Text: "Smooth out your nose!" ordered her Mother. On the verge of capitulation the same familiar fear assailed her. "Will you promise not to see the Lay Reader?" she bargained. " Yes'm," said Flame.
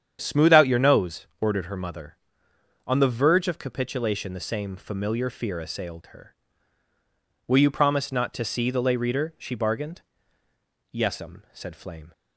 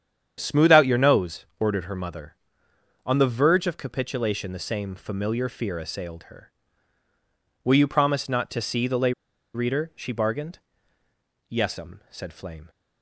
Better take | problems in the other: first | starts louder than the rest; strong; until 1.3 s; 8.5 dB; strong in the first // pauses between "Lay" and "Reader"; at 9.1 s; 0.43 s long

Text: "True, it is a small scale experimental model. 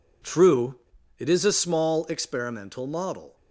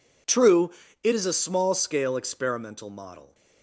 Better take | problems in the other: second | skips "scale"; at 2.0 s

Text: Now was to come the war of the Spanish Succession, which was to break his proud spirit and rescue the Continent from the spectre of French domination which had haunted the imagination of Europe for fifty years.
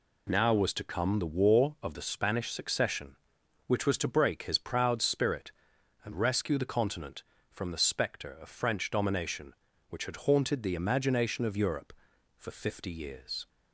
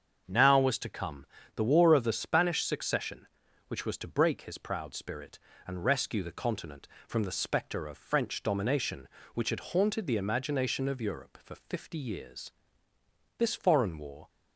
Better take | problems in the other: first | starts louder than the rest; until 1.2 s; 7 dB // pauses between "come" and "the"; slight; at 1.2 s; 0.28 s long // goes on to say "This foreign war"; noticeable; from 13.3 s on; 0.92 s long

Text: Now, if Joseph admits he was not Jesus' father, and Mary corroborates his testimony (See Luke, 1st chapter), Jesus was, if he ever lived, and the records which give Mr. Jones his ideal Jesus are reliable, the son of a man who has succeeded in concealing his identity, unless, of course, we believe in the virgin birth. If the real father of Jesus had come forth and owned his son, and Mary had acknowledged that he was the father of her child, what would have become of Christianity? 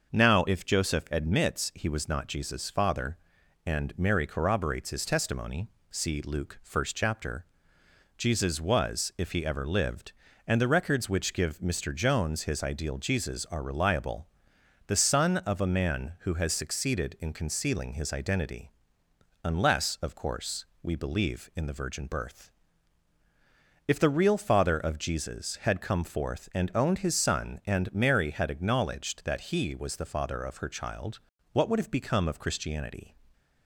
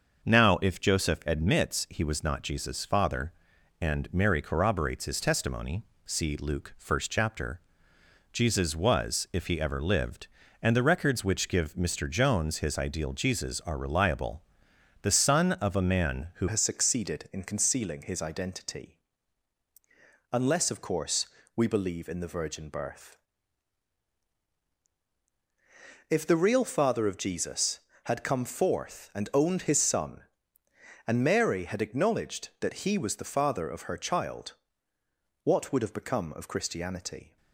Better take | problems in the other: first | starts louder than the rest; noticeable; until 1.2 s; 6 dB; noticeable in the first // changes voice at "has"; from 16.4 s on; 20.9 s long

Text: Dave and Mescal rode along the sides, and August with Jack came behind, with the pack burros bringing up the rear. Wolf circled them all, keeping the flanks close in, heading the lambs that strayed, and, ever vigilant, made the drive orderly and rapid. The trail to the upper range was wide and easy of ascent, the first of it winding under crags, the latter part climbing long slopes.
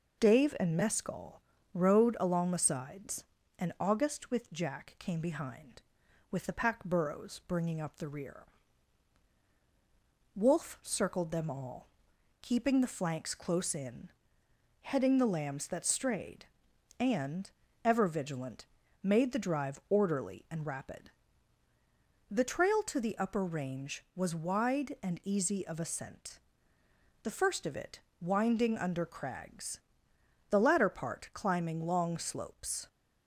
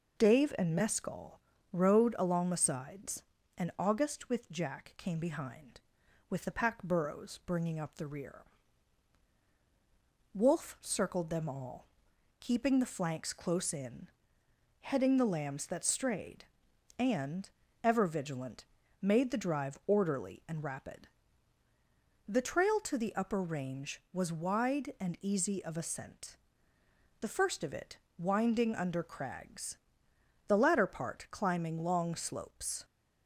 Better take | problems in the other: neither | pauses between "Mescal" and "rode"; slight; the same in both // pauses between "it" and "winding"; slight; the same in both

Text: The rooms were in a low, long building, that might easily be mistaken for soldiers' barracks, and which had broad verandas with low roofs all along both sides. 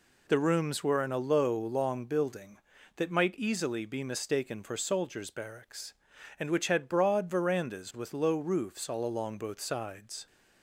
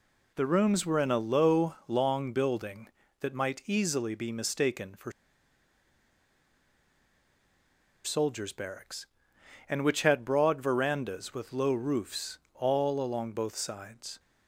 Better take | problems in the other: first | pauses between "for" and "soldiers"; strong; at 5.1 s; 2.9 s long // pauses between "roofs" and "all"; slight; at 12.3 s; 0.16 s long

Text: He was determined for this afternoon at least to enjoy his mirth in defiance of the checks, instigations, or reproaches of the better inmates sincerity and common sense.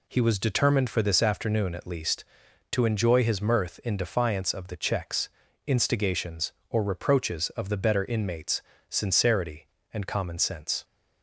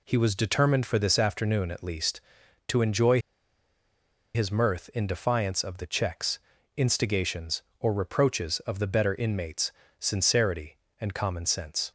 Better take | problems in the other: first | pauses between "enjoy" and "his"; at 3.1 s; 1.1 s long // pauses between "inmates" and "sincerity"; slight; at 9.7 s; 0.28 s long; slight in the first

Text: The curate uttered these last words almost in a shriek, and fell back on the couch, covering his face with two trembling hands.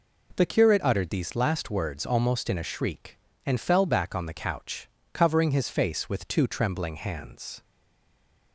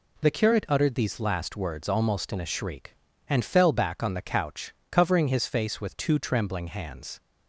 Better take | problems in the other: second | stays silent after the last word; slight; from 7.6 s on; 0.9 s long

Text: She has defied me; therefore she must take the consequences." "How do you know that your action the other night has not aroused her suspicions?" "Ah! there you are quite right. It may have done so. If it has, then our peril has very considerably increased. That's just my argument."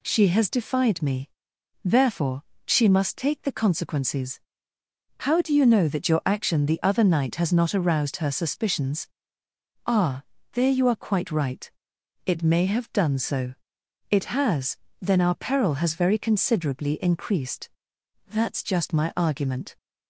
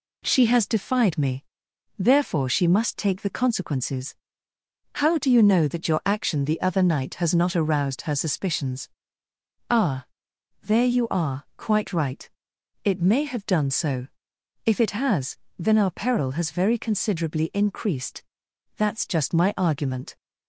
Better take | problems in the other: second | pauses between "therefore" and "she"; slight; at 2.4 s; 0.22 s long // skips "If"; at 13.8 s

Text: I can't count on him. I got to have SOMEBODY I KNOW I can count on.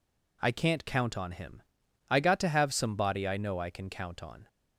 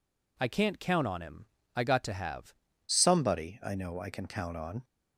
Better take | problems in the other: first | changes voice at "SOMEBODY"; from 2.8 s on; 2.0 s long

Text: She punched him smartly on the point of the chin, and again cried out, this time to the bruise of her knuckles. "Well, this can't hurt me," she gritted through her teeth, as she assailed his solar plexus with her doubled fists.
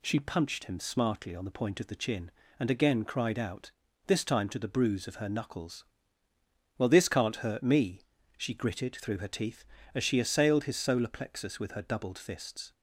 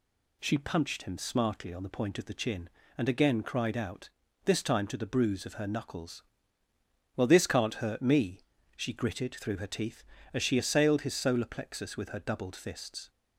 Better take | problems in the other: neither | none

